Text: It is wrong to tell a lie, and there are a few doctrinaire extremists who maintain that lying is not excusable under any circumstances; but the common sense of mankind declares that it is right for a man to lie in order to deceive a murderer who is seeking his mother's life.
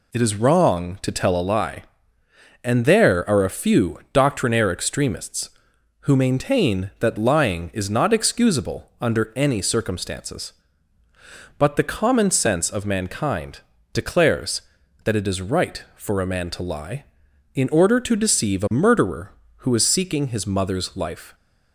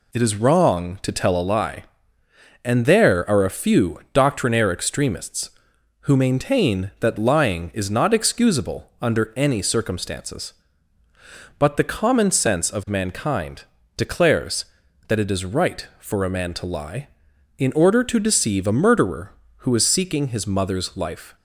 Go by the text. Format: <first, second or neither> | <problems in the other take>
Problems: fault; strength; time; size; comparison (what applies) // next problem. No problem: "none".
neither | pauses between "mankind" and "declares"; slight; the same in both